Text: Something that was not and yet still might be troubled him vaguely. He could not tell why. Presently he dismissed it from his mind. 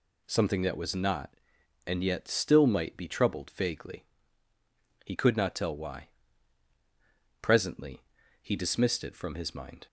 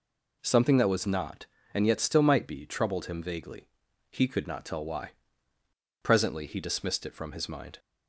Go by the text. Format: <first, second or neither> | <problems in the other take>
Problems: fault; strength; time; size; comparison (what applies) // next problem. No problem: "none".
second | skips "him"; at 3.4 s // pauses between "Presently" and "he"; at 8.0 s; 0.38 s long